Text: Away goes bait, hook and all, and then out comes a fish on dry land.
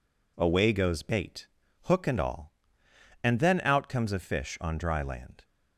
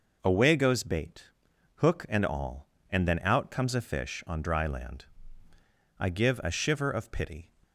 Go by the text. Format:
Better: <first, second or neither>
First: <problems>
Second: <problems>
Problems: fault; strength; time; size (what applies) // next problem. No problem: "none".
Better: first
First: none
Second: goes on to say "I give a shiver of pity"; from 5.9 s on; 1.5 s long